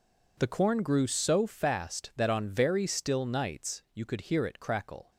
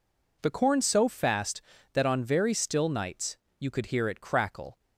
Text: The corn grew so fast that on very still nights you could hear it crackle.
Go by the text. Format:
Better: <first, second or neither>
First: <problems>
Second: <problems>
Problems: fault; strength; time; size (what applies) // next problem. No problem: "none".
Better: first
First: none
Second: skips "grew"; at 0.8 s // pauses between "nights" and "you"; slight; at 3.3 s; 0.22 s long